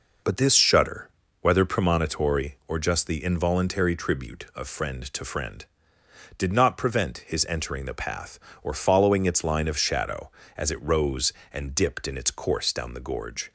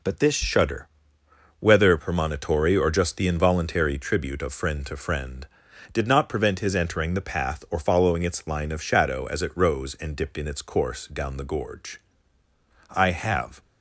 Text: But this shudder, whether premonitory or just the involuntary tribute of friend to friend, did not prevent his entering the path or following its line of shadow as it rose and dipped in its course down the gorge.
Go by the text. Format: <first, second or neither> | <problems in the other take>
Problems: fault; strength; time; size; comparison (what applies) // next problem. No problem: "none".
first | goes on to say "I have"; noticeable; from 12.9 s on; 0.68 s long